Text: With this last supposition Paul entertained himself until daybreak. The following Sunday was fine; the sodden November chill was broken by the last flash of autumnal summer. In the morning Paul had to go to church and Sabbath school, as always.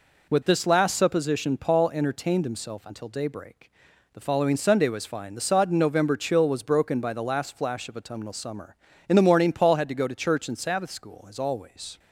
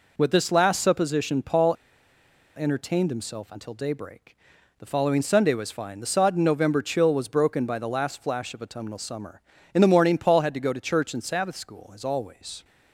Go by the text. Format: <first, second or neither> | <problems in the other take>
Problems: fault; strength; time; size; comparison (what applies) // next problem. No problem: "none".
first | pauses between "Paul" and "entertained"; noticeable; at 1.7 s; 0.80 s long